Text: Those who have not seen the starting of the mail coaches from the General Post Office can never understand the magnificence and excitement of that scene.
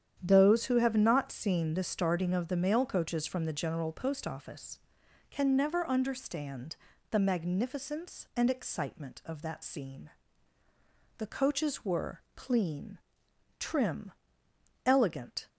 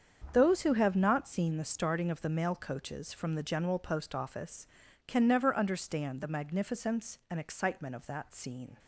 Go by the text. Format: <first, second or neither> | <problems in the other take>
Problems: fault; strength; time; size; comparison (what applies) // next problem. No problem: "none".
second | starts louder than the rest; strong; until 1.2 s; 9 dB; strong in the second // pauses between "understand" and "the"; slight; at 6.7 s; 0.36 s long // goes on to say "The coaches were clean trim elegant"; strong; from 11.1 s on; 4.3 s long